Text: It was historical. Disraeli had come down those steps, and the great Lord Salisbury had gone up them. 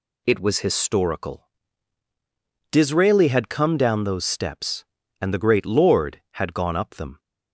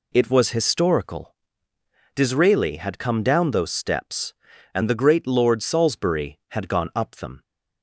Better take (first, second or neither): second